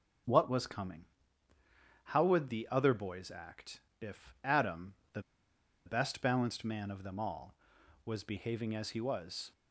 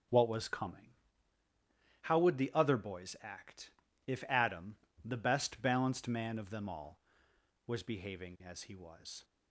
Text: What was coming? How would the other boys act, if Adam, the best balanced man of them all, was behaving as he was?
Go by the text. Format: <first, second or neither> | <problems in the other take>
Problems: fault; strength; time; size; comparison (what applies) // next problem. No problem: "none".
second | starts louder than the rest; strong; until 2.2 s; 7.5 dB; also in the second // pauses between "the" and "best"; noticeable; at 5.2 s; 0.65 s long